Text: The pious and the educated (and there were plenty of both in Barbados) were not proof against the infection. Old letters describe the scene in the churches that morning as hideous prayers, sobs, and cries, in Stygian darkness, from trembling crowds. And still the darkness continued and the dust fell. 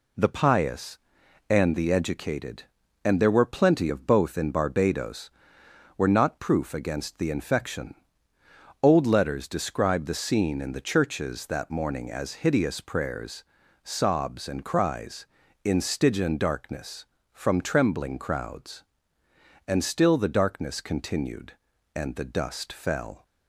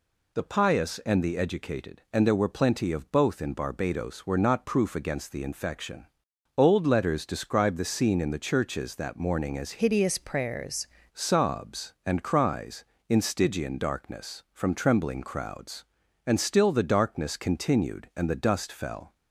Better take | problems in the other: first | changes voice from "hideous" to "prayers"; from 9.8 to 10.8 s; 1.0 s long

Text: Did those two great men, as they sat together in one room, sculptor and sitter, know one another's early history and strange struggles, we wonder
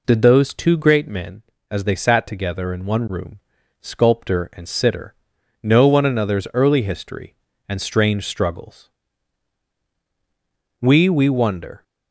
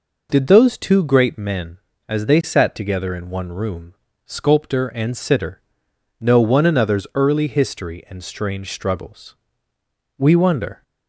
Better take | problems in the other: second | says "we" twice; at 11.0 s

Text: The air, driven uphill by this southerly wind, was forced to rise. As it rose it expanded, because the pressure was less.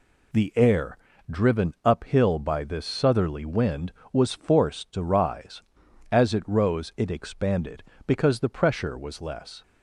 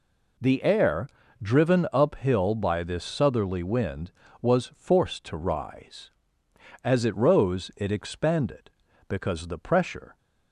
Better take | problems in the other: first | stops before "was less"; at 10.1 s

